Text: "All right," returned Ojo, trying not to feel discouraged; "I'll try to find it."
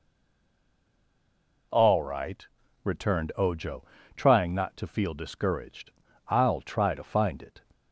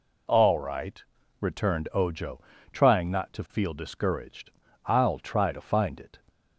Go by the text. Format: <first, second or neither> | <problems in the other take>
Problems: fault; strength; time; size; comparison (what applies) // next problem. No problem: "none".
second | stays silent before the first word; noticeable; until 1.7 s; 1.7 s long